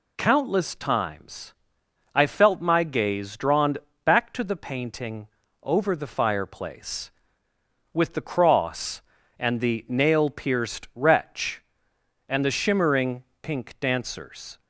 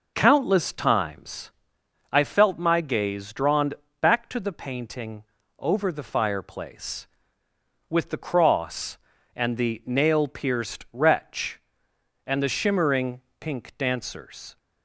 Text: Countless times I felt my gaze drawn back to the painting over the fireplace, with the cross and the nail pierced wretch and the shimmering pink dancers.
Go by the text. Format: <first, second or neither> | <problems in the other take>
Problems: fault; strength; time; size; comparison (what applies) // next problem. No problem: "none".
first | starts louder than the rest; noticeable; until 1.6 s; 5 dB // pauses between "times" and "I"; noticeable; at 1.5 s; 0.60 s long; noticeable in the first // pauses between "drawn" and "back"; slight; at 3.7 s; 0.26 s long; slight in the first // pauses between "painting" and "over"; slight; at 5.2 s; 0.36 s long; slight in the first // pauses between "shimmering" and "pink"; slight; at 13.2 s; 0.18 s long; slight in the first